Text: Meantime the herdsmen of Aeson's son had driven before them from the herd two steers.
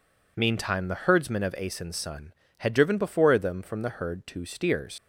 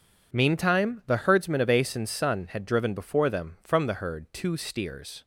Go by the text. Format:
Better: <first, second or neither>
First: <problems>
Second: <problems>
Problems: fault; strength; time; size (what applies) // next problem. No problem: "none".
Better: second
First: leaves "steers" unfinished; at 4.9 s; 75 ms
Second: none